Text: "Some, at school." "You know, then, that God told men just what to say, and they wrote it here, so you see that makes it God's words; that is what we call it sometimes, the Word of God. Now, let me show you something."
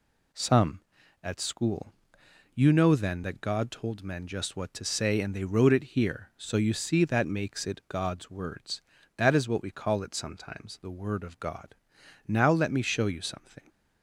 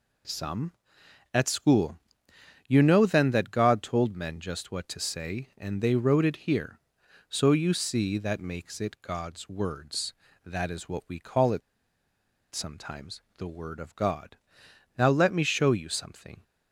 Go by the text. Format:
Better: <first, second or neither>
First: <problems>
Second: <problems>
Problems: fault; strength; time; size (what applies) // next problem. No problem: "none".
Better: first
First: none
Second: pauses between "it" and "sometimes"; noticeable; at 11.6 s; 0.93 s long